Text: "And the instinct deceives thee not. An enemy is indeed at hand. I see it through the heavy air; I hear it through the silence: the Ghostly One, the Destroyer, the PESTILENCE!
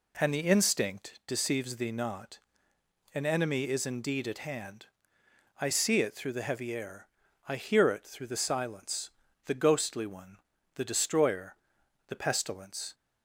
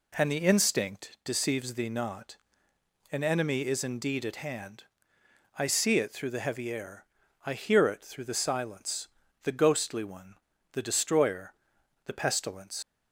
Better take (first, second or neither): first